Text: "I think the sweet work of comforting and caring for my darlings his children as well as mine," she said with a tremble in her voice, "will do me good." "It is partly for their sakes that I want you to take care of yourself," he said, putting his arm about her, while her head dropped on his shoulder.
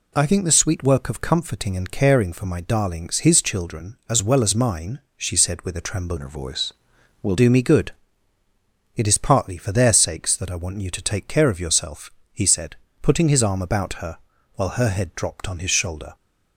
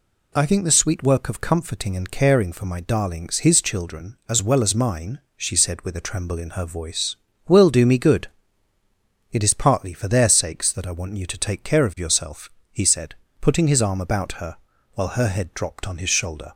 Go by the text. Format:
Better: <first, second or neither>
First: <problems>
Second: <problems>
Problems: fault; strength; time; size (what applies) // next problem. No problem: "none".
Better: second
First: changes voice from "in" to "will"; from 6.1 to 7.3 s; 1.2 s long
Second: none